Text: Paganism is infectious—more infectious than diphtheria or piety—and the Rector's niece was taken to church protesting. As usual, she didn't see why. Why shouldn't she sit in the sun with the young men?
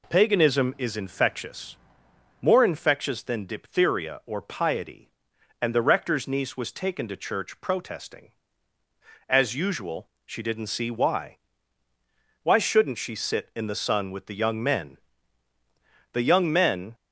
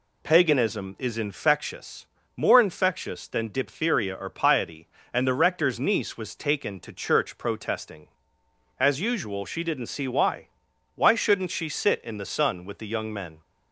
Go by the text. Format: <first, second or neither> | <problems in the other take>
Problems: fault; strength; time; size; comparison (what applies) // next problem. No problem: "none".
second | goes on to say "The young men"; noticeable; from 16.1 s on; 0.82 s long